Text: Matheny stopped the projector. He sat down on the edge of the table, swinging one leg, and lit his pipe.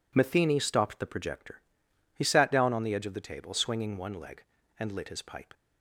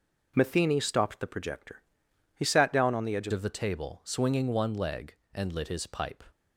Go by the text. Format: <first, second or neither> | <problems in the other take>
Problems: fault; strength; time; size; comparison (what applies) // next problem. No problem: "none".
first | changes voice at "of"; from 3.3 s on; 2.9 s long